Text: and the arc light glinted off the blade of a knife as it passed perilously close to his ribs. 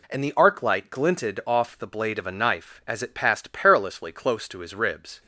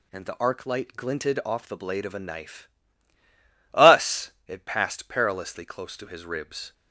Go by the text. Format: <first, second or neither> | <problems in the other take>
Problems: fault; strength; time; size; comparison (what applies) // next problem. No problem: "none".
first | says "us" for "as"; at 3.7 s